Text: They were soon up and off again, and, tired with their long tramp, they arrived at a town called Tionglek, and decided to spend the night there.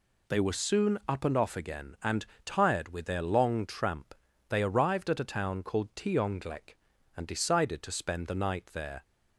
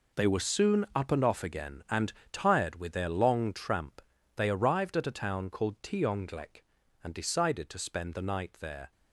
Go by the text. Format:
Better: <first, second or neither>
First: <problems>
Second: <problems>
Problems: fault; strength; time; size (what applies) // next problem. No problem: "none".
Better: first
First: none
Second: gets quieter; strong; throughout; 11.5 dB